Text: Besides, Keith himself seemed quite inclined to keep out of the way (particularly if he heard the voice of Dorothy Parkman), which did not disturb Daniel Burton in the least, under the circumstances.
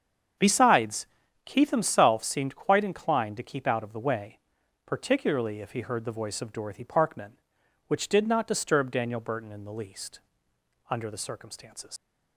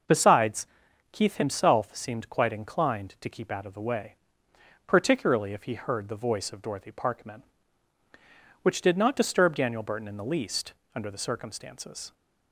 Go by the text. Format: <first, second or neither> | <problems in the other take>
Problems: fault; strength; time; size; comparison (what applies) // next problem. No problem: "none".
second | starts louder than the rest; strong; until 1.7 s; 7.5 dB // leaves "circumstances" unfinished; at 11.9 s; 125 ms